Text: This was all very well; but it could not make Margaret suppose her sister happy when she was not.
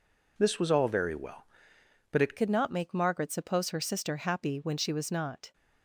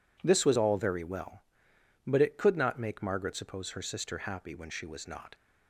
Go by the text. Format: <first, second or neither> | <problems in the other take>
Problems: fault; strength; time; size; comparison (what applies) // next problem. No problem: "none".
second | changes voice at "could"; from 2.3 s on; 3.2 s long